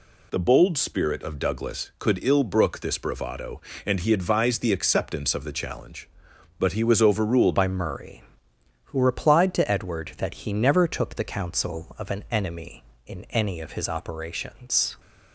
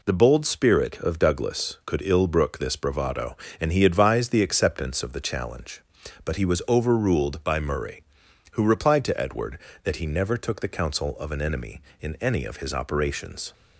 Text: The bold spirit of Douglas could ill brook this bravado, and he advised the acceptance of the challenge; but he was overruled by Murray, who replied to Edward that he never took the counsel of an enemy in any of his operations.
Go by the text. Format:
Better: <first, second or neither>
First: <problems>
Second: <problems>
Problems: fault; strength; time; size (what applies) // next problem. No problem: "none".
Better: second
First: changes voice at "by"; from 7.5 s on; 7.4 s long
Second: none